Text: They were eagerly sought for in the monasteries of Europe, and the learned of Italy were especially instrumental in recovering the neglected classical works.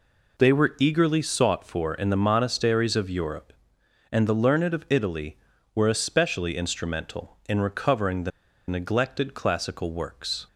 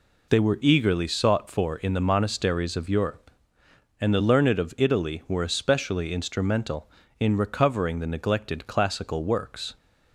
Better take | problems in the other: second | pauses between "the" and "neglected"; at 8.3 s; 0.38 s long

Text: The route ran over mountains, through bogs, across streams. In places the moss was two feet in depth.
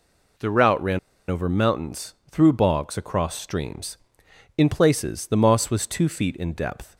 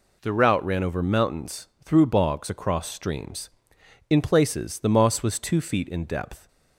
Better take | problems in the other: second | pauses between "ran" and "over"; slight; at 0.9 s; 0.30 s long

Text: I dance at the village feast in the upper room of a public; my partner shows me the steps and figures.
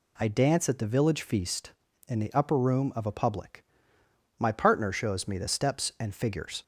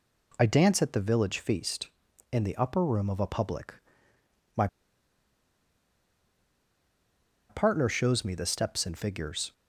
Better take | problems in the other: first | pauses between "my" and "partner"; strong; at 4.6 s; 2.8 s long

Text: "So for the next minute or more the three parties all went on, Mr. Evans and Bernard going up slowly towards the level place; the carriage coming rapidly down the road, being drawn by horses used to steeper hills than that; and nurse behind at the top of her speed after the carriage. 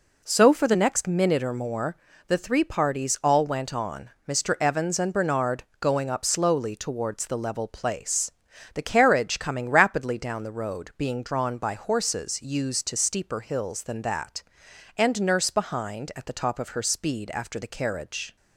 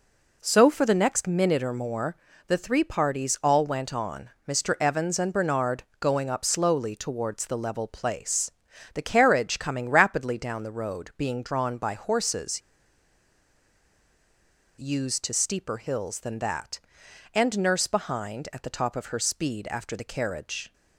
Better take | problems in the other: first | pauses between "more" and "the"; slight; at 2.1 s; 0.32 s long; slight in the first // pauses between "Bernard" and "going"; slight; at 5.8 s; 0.16 s long; slight in the first // pauses between "horses" and "used"; strong; at 12.6 s; 2.1 s long

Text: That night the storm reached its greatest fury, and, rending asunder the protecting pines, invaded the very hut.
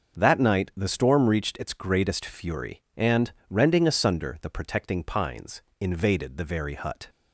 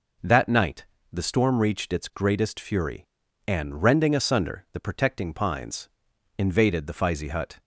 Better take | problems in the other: first | pauses between "night" and "the"; slight; at 0.8 s; 0.28 s long // says "fizey" for "very"; at 6.9 s

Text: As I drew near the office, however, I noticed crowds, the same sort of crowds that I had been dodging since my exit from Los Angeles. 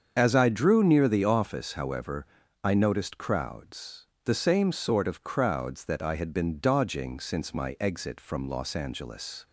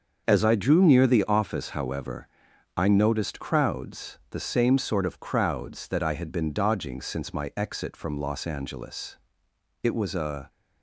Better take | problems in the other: first | starts louder than the rest; until 1.2 s; 6.5 dB; also in the first // goes on to say "It was a"; noticeable; from 9.8 s on; 0.66 s long

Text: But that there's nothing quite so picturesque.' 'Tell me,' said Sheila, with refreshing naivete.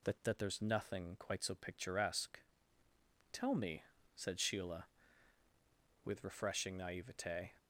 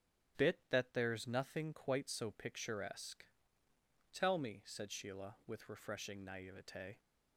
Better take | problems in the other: first | starts louder than the rest; strong; until 1.5 s; 11.5 dB // says "Bit" for "But"; at 0.3 s

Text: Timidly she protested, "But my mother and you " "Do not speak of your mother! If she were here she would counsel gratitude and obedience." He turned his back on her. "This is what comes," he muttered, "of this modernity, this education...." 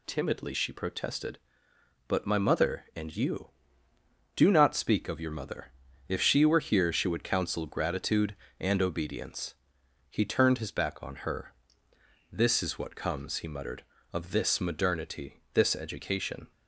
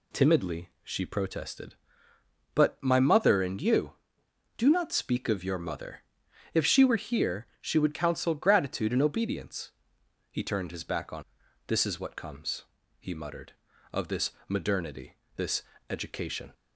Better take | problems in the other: first | skips "her"; at 11.4 s // pauses between "this" and "modernity"; slight; at 14.3 s; 0.16 s long // pauses between "this" and "education"; slight; at 15.6 s; 0.26 s long

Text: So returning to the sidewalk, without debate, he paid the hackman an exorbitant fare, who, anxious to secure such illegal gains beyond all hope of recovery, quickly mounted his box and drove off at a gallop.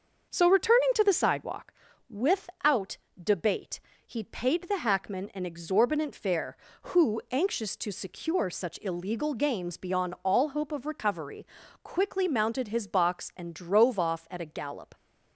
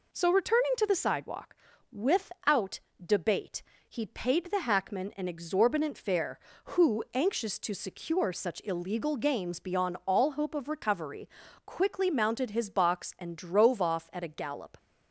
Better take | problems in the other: second | starts louder than the rest; until 1.8 s; 6.5 dB // pauses between "without" and "debate"; slight; at 2.9 s; 0.22 s long; slight in the second

